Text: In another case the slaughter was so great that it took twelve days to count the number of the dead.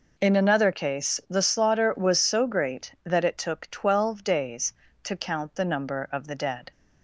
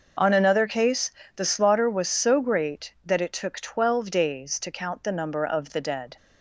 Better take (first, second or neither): first